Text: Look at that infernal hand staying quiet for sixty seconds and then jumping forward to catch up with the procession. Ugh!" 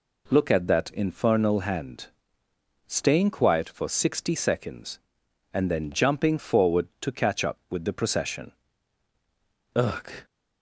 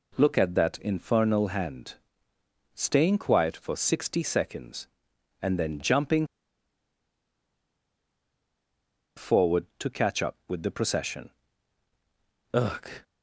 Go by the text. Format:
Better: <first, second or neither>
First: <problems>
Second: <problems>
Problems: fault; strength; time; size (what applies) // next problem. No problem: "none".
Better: first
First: pauses between "hand" and "staying"; noticeable; at 2.0 s; 0.80 s long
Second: pauses between "hand" and "staying"; noticeable; at 1.9 s; 0.80 s long // pauses between "jumping" and "forward"; strong; at 6.2 s; 2.9 s long